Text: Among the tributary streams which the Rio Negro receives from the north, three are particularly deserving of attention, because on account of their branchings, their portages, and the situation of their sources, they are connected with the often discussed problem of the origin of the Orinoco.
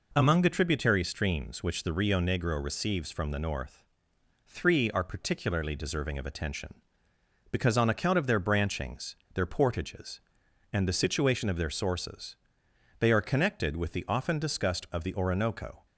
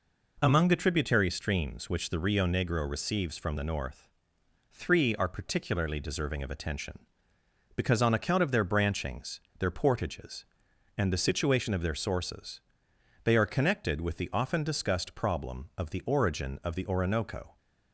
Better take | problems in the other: second | skips "problem of the origin"; at 14.9 s

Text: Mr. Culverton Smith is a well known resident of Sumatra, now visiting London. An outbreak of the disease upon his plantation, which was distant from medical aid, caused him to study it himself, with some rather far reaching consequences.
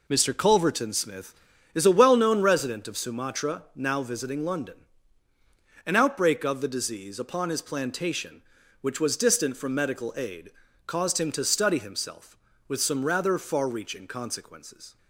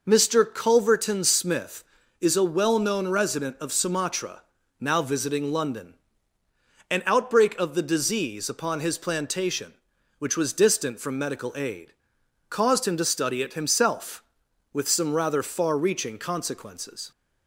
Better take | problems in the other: second | skips "it"; at 11.7 s

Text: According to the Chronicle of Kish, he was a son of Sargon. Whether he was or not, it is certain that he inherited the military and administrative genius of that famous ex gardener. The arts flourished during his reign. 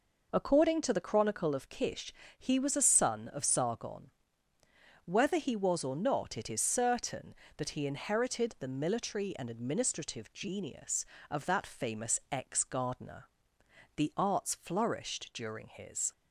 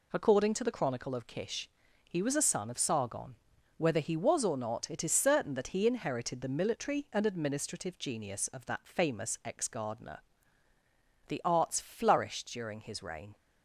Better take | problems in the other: second | stops before "reign"; at 16.1 s

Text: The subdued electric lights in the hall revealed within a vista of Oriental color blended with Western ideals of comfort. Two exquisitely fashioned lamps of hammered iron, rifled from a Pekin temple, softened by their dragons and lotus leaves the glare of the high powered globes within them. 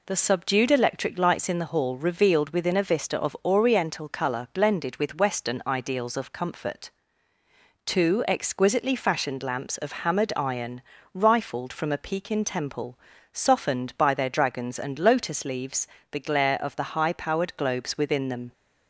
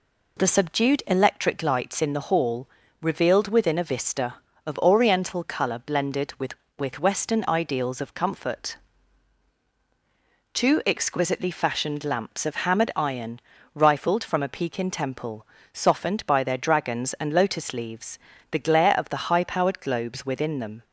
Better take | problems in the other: first | pauses between "hall" and "revealed"; slight; at 2.6 s; 0.34 s long // says "with" twice; at 6.7 s // pauses between "leaves" and "the"; slight; at 18.1 s; 0.32 s long; slight in the first

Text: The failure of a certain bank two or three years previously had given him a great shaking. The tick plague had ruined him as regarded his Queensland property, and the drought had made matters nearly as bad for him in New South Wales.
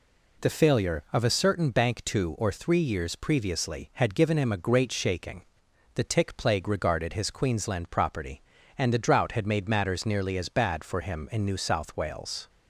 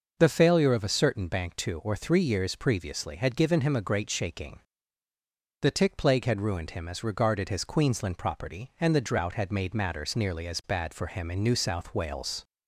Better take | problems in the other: second | skips "had ruined him as"; at 6.6 s

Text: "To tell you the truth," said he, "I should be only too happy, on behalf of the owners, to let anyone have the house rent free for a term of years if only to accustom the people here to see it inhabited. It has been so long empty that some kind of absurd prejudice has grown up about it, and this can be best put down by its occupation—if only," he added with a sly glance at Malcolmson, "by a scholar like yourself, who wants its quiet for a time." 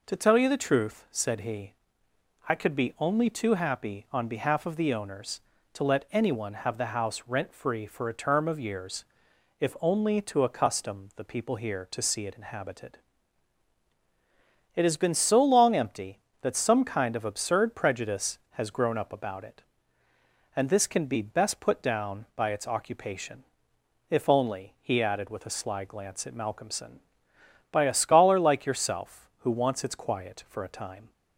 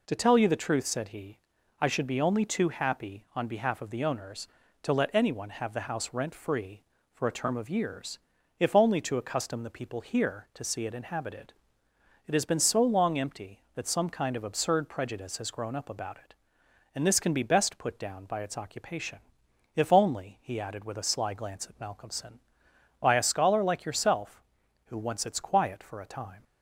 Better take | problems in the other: second | says "could" for "should"; at 2.5 s // pauses between "years" and "if"; noticeable; at 9.0 s; 0.56 s long; also in the second

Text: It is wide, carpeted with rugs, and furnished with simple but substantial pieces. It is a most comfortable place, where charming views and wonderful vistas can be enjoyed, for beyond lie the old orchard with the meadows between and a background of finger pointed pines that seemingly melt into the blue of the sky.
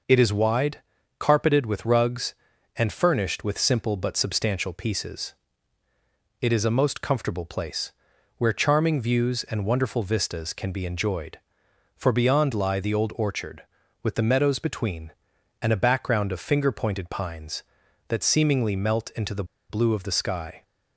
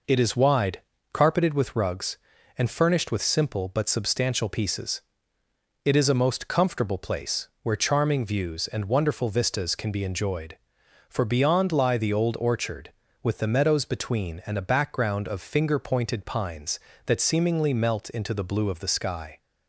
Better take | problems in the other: second | pauses between "the" and "blue"; slight; at 19.4 s; 0.26 s long

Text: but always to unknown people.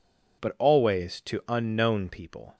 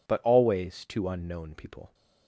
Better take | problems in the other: neither | none

